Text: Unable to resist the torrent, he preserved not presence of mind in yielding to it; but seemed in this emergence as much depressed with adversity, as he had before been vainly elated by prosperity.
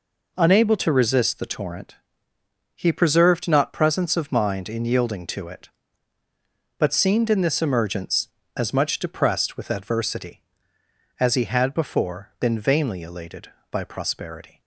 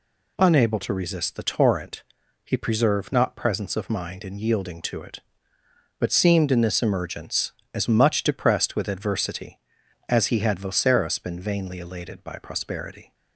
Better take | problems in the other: first | says "voceros" for "before"; at 10.5 s

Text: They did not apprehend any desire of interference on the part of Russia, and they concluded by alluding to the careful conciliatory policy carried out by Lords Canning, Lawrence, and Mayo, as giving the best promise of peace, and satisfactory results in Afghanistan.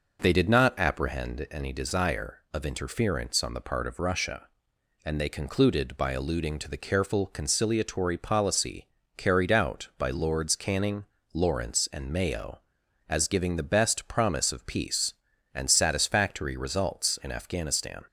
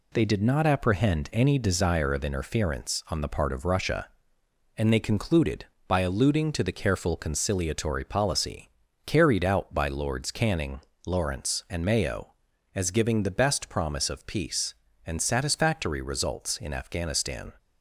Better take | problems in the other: neither | pauses between "policy" and "carried"; slight; the same in both

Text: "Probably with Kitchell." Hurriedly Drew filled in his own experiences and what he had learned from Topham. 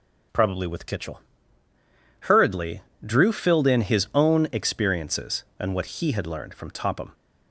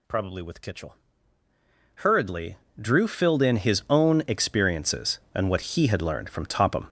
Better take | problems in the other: first | gets louder; strong; throughout; 10 dB // pauses between "Hurriedly" and "Drew"; slight; at 2.5 s; 0.20 s long; slight in the first

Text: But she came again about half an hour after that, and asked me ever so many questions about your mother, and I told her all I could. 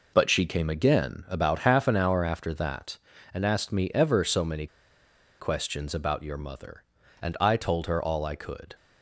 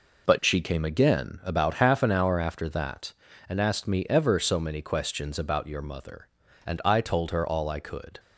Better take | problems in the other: second | pauses between "many" and "questions"; noticeable; at 4.6 s; 0.73 s long

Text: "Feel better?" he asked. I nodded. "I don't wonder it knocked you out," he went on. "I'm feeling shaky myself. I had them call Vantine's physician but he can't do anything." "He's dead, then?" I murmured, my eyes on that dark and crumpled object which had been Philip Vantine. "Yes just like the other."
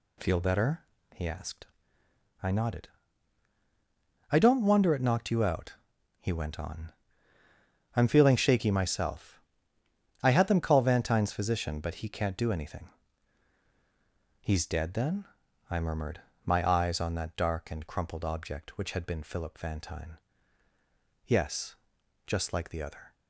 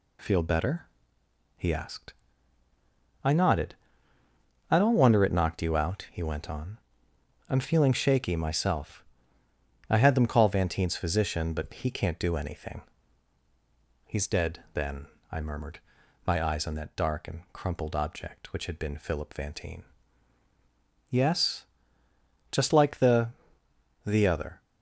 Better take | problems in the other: first | pauses between "Yes" and "just"; noticeable; at 21.6 s; 0.86 s long; noticeable in the first // says "the" twice; at 24.0 s

